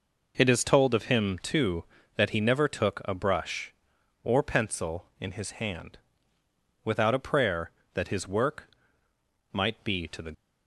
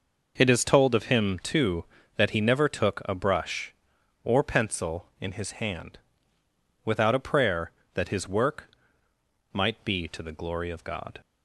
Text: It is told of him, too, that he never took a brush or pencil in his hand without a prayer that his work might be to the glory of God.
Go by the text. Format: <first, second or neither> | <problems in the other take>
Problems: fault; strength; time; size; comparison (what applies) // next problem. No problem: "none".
second | pauses between "hand" and "without"; noticeable; at 5.9 s; 0.86 s long; noticeable in the second // pauses between "work" and "might"; noticeable; at 8.6 s; 0.84 s long; noticeable in the second // stops before "glory of God"; at 10.3 s